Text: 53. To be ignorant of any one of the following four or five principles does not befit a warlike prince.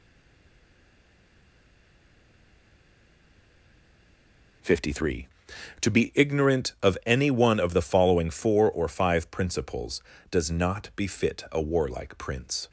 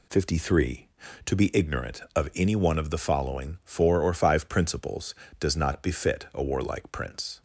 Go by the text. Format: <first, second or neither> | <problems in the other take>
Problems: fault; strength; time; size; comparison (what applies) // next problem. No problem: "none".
second | stays silent before the first word; strong; until 4.6 s; 4.6 s long